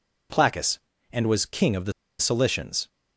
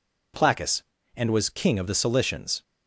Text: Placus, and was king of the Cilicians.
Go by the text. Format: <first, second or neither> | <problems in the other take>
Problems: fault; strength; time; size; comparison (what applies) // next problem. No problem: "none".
second | pauses between "the" and "Cilicians"; slight; at 1.9 s; 0.28 s long